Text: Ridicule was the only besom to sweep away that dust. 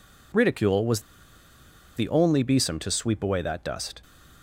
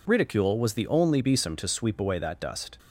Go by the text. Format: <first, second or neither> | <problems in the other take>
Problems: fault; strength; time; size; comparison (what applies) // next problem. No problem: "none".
second | pauses between "was" and "the"; noticeable; at 1.0 s; 0.95 s long